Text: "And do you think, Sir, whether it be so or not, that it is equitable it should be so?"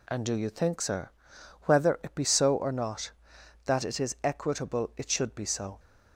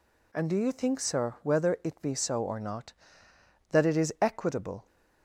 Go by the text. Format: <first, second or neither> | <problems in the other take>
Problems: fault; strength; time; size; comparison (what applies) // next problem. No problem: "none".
first | stops before "it should be so"; at 4.8 s